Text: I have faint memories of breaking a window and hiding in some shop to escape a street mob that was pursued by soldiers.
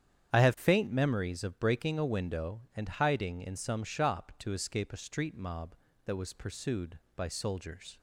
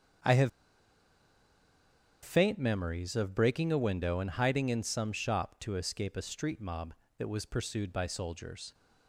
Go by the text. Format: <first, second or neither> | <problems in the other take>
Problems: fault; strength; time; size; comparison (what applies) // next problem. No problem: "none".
first | starts louder than the rest; strong; until 2.9 s; 7.5 dB; strong in the first // pauses between "have" and "faint"; strong; at 0.4 s; 1.7 s long